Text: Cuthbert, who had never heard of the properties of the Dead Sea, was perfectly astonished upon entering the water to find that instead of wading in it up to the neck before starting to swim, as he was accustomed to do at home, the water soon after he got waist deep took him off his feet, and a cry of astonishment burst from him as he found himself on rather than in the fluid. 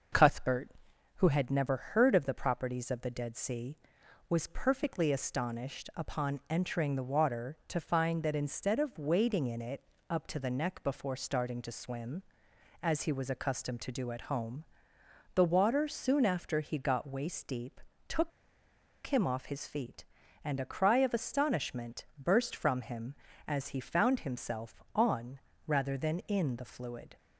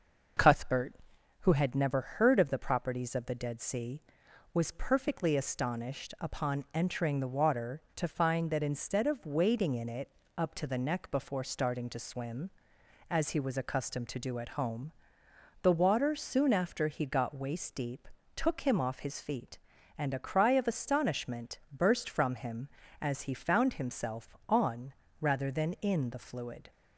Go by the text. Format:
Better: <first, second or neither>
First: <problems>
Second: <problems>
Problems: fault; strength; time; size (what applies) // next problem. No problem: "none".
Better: second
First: starts louder than the rest; until 1.6 s; 6 dB // pauses between "it" and "up"; slight; at 9.8 s; 0.28 s long // pauses between "deep" and "took"; slight; at 17.7 s; 0.28 s long // pauses between "took" and "him"; noticeable; at 18.3 s; 0.76 s long // pauses between "on" and "rather"; slight; at 25.3 s; 0.26 s long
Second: starts louder than the rest; until 1.8 s; 6 dB // pauses between "it" and "up"; slight; at 10.0 s; 0.28 s long // pauses between "deep" and "took"; slight; at 18.0 s; 0.28 s long // pauses between "on" and "rather"; slight; at 24.9 s; 0.26 s long